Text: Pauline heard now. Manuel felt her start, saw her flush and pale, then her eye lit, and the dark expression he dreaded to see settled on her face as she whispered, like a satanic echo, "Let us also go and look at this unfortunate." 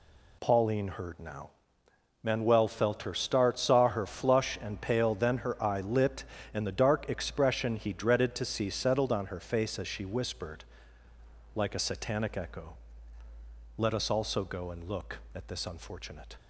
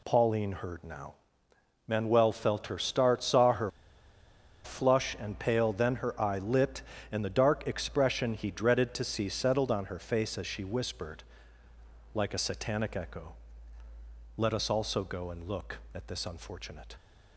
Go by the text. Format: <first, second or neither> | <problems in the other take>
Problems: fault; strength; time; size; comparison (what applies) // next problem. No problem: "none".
first | pauses between "her" and "flush"; noticeable; at 3.6 s; 0.95 s long